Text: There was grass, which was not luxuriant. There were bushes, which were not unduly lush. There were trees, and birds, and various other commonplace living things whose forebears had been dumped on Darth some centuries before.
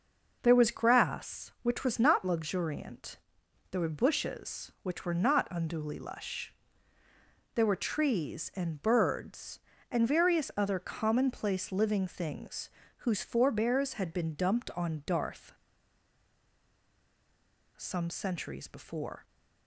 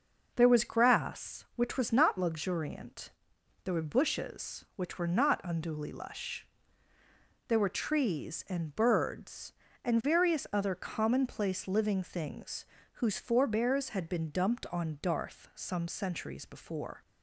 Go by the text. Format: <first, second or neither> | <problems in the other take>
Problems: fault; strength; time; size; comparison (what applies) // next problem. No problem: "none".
second | pauses between "things" and "whose"; slight; at 12.6 s; 0.30 s long; slight in the second // pauses between "Darth" and "some"; strong; at 15.5 s; 2.2 s long